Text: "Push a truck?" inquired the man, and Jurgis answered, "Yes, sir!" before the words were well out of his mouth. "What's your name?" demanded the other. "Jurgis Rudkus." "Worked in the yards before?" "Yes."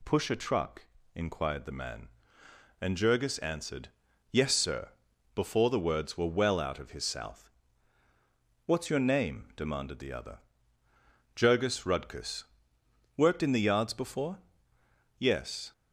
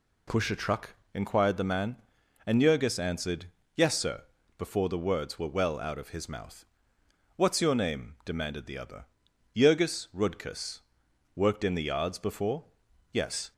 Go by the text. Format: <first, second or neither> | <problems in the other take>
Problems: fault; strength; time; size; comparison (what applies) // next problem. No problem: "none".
second | says "south" for "mouth"; at 7.0 s